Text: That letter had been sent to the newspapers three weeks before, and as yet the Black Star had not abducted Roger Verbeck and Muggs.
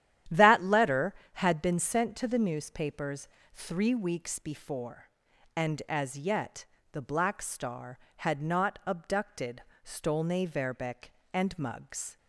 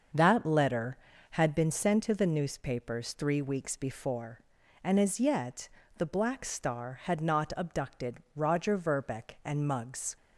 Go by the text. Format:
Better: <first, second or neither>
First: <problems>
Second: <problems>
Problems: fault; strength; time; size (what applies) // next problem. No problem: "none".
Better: second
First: starts louder than the rest; strong; until 1.5 s; 11 dB // pauses between "newspapers" and "three"; slight; at 3.2 s; 0.26 s long // pauses between "yet" and "the"; slight; at 6.6 s; 0.26 s long // says "Stolne" for "Roger"; at 9.8 s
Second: starts louder than the rest; until 1.4 s; 6.5 dB // pauses between "yet" and "the"; slight; at 5.6 s; 0.26 s long